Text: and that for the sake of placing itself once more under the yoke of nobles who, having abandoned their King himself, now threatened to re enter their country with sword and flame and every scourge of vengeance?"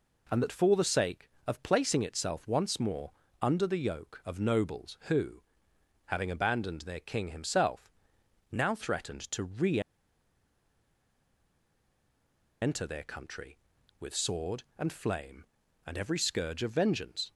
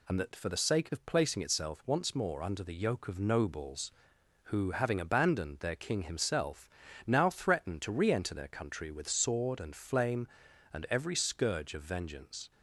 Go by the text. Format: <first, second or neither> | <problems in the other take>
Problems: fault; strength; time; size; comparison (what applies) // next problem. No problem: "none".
second | pauses between "more" and "under"; slight; at 3.1 s; 0.30 s long // pauses between "re" and "enter"; strong; at 9.7 s; 2.8 s long